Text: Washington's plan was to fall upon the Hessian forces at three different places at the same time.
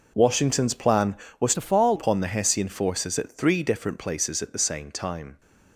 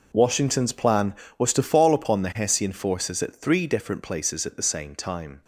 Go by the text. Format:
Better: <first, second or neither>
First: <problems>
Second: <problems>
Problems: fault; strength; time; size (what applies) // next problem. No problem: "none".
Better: second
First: changes voice from "to" to "fall"; from 1.5 to 1.9 s; 0.4 s long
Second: none